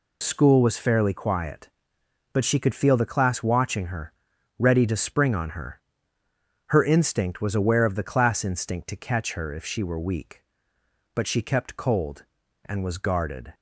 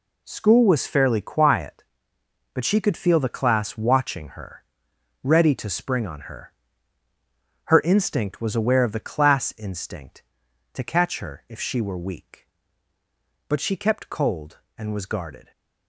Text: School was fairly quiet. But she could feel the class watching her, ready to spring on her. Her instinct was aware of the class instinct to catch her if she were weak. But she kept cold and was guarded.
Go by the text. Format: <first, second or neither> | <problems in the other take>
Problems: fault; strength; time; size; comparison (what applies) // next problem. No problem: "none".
neither | none